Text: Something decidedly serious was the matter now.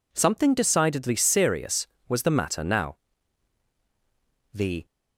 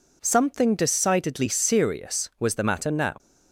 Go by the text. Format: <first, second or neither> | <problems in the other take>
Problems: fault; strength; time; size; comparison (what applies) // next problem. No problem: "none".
second | goes on to say "The"; slight; from 4.5 s on; 0.32 s long